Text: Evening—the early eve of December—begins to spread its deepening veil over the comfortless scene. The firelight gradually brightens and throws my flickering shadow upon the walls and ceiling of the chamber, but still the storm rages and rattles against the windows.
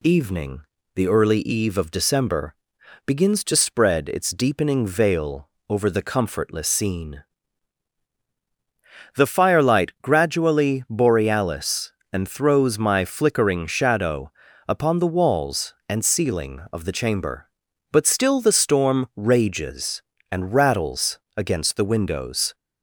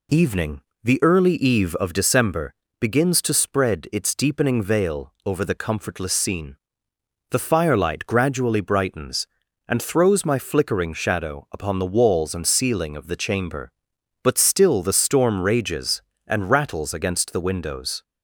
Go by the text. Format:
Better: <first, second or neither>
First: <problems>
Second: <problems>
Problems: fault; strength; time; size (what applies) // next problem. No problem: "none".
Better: second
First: pauses between "veil" and "over"; slight; at 5.4 s; 0.20 s long // says "borealis" for "brightens"; at 10.9 s // pauses between "shadow" and "upon"; slight; at 14.3 s; 0.34 s long // pauses between "rattles" and "against"; slight; at 21.1 s; 0.18 s long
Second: none